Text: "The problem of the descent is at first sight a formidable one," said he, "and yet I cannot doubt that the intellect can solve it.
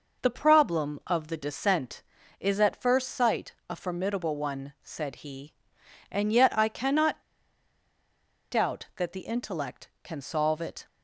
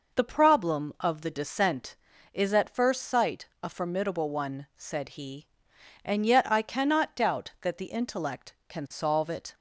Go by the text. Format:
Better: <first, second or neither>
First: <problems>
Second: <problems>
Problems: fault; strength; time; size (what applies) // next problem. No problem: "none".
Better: second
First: pauses between "sight" and "a"; slight; at 3.5 s; 0.16 s long // pauses between "cannot" and "doubt"; strong; at 7.2 s; 1.2 s long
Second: pauses between "sight" and "a"; slight; at 3.4 s; 0.16 s long